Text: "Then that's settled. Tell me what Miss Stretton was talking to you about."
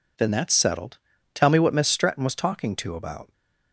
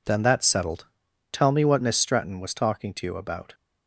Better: second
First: skips "you"; at 2.9 s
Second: none

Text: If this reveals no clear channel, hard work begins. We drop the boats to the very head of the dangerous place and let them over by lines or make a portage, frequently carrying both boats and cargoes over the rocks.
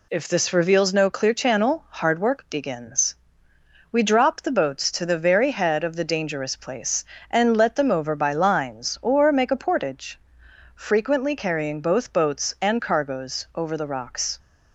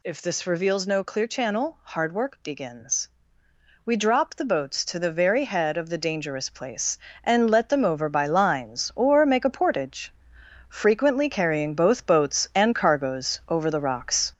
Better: first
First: none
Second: gets louder; noticeable; throughout; 5.5 dB

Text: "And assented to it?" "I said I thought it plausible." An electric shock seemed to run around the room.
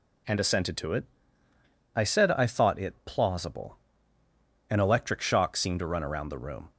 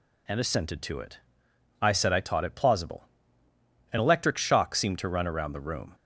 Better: first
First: none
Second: says "taught" for "thought"; at 2.1 s

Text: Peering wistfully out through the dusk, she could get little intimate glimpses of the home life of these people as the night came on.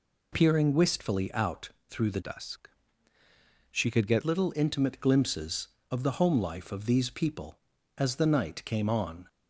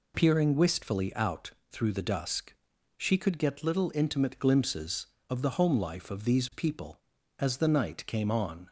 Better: second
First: pauses between "out" and "through"; slight; at 1.6 s; 0.18 s long // changes voice from "dusk" to "get"; from 2.2 to 4.2 s; 2.0 s long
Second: pauses between "out" and "through"; slight; at 1.5 s; 0.18 s long

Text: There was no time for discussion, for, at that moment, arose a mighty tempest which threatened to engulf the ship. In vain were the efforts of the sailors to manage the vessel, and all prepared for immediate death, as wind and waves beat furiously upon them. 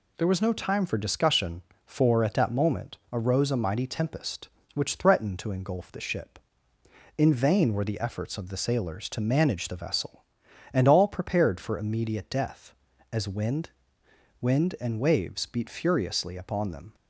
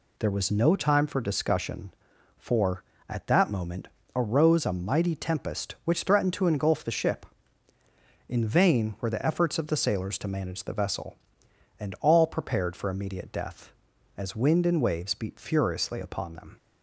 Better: second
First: says "wind" twice; at 14.4 s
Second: none

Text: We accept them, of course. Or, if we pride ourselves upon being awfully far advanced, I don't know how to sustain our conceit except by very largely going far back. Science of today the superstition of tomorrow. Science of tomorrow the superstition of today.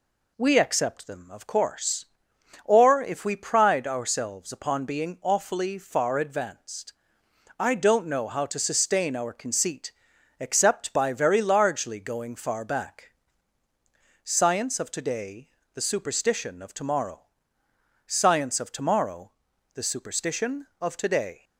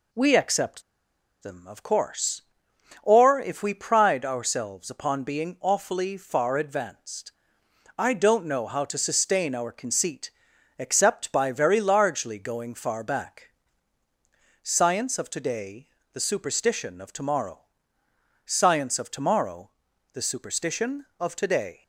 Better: first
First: pauses between "conceit" and "except"; noticeable; at 9.9 s; 0.48 s long // pauses between "today" and "the"; slight; at 15.4 s; 0.26 s long // pauses between "tomorrow" and "the"; at 19.3 s; 0.42 s long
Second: pauses between "accept" and "them"; noticeable; at 0.8 s; 0.60 s long // pauses between "conceit" and "except"; noticeable; at 10.3 s; 0.48 s long // pauses between "today" and "the"; slight; at 15.8 s; 0.26 s long // pauses between "tomorrow" and "the"; at 19.7 s; 0.42 s long

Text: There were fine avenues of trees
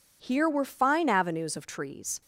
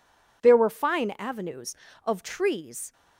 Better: second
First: says "Here" for "There"; at 0.2 s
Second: none

